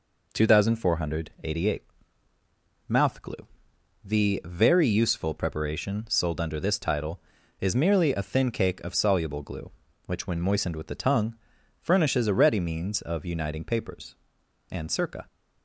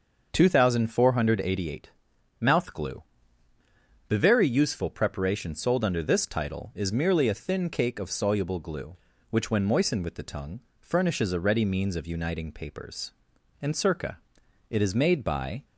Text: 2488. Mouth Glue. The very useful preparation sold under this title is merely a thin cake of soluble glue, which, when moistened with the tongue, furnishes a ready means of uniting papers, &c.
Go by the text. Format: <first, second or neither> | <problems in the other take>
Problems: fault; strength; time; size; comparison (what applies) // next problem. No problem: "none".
first | starts louder than the rest; until 1.3 s; 6.5 dB // goes on to say "It is made by"; noticeable; from 14.6 s on; 0.96 s long